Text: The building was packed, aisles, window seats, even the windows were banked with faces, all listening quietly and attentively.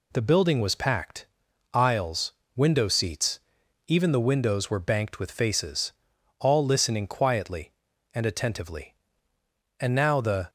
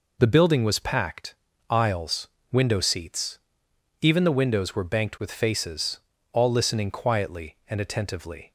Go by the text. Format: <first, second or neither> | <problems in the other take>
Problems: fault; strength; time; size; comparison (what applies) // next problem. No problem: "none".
second | goes on to say "And now the"; noticeable; from 9.7 s on; 0.70 s long